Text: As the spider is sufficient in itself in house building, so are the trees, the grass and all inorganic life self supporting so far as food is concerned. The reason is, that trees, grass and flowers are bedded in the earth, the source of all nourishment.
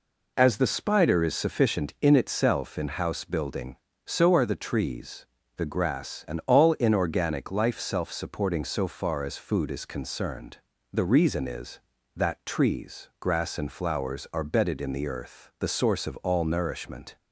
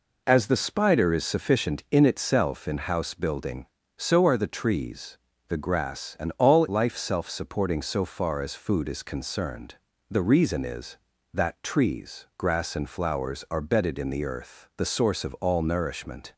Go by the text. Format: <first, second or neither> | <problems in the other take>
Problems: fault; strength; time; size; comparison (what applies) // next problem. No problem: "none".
first | skips "inorganic"; at 6.6 s